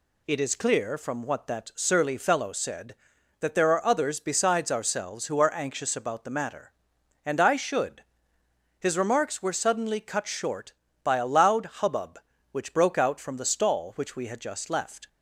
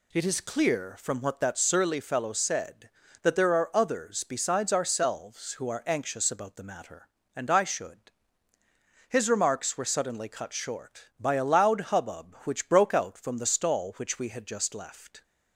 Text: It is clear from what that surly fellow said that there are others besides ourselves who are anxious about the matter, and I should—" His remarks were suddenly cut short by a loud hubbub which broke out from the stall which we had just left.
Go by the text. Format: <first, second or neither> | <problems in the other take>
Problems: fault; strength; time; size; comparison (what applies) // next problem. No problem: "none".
neither | none